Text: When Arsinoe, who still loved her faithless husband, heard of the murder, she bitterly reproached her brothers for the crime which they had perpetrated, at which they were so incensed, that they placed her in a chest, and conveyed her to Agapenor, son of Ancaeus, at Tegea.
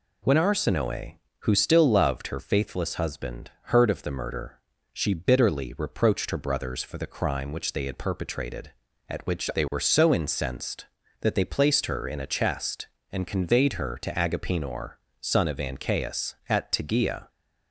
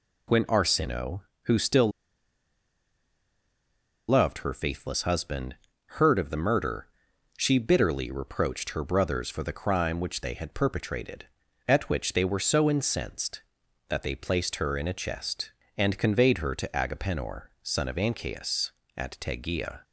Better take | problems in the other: first | pauses between "still" and "loved"; strong; at 1.8 s; 2.1 s long

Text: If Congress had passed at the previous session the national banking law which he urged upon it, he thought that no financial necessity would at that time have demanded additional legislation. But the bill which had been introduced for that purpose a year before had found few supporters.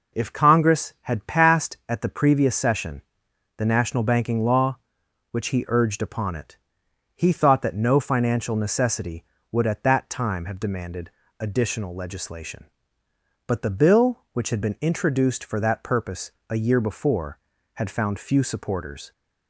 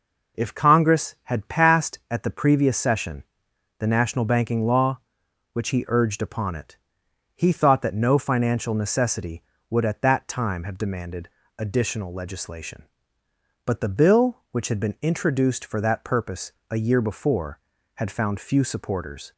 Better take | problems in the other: neither | pauses between "session" and "the"; noticeable; the same in both // pauses between "demanded" and "additional"; slight; the same in both // pauses between "purpose" and "a"; slight; the same in both

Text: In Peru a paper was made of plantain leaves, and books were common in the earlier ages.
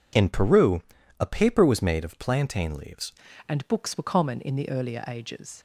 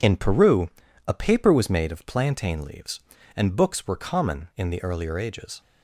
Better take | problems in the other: second | pauses between "Peru" and "a"; at 0.7 s; 0.38 s long; also in the second // changes voice at "and"; from 3.4 s on; 2.1 s long

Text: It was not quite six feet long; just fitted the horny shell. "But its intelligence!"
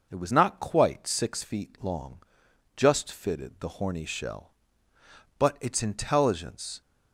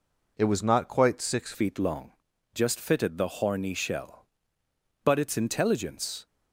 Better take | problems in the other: first | changes voice at "feet"; from 1.5 s on; 4.7 s long

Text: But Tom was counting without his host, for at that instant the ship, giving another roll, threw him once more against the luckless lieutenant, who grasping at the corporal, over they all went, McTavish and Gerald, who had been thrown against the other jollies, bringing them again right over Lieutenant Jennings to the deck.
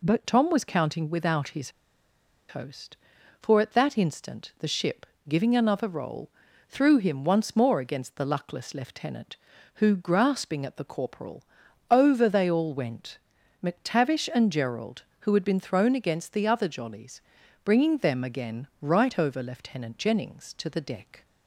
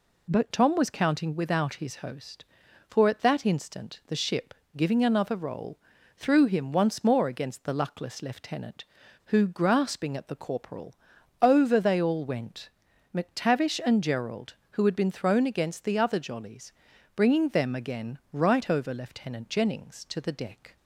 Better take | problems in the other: second | pauses between "his" and "host"; noticeable; at 1.7 s; 0.77 s long

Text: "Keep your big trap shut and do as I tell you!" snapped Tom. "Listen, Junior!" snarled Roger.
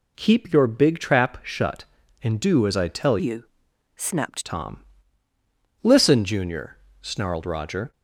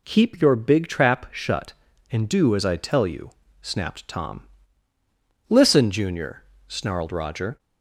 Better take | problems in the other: second | changes voice from "you" to "snapped"; from 3.1 to 4.4 s; 1.3 s long

